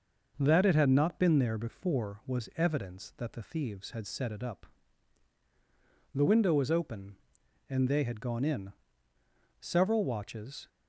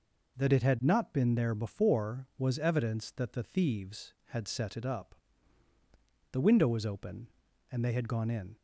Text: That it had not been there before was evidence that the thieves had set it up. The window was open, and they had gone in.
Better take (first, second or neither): second